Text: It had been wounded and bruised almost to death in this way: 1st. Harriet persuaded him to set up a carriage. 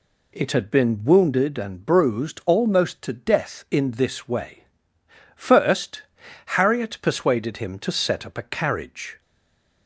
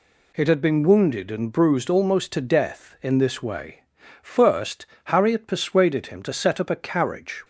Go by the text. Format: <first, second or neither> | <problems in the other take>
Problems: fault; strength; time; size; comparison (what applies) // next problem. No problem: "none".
second | stays silent after the last word; slight; from 9.2 s on; 0.6 s long